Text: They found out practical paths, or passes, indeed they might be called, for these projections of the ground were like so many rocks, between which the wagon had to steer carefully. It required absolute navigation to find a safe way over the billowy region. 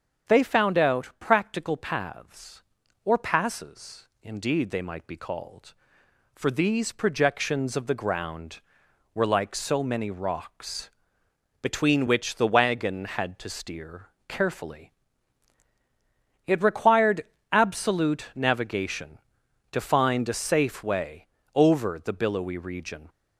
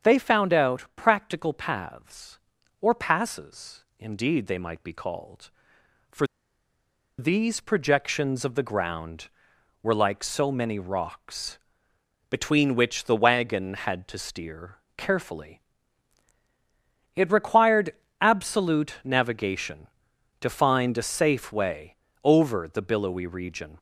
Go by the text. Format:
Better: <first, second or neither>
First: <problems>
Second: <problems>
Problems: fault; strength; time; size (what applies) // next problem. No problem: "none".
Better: first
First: starts louder than the rest; strong; until 1.3 s; 8 dB // pauses between "steer" and "carefully"; slight; at 14.0 s; 0.20 s long // pauses between "required" and "absolute"; slight; at 17.2 s; 0.26 s long // pauses between "way" and "over"; slight; at 21.2 s; 0.26 s long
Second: starts louder than the rest; strong; until 1.1 s; 8 dB // pauses between "for" and "these"; noticeable; at 6.2 s; 0.92 s long // pauses between "steer" and "carefully"; slight; at 14.7 s; 0.20 s long // pauses between "required" and "absolute"; slight; at 17.9 s; 0.26 s long // pauses between "way" and "over"; slight; at 21.9 s; 0.26 s long